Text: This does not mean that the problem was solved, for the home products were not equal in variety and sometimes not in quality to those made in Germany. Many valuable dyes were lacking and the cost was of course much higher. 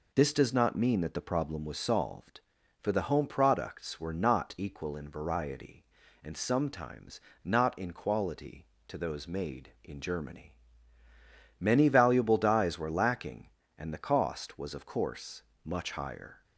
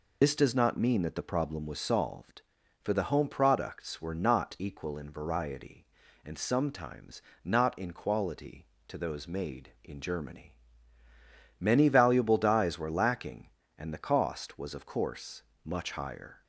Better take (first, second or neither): first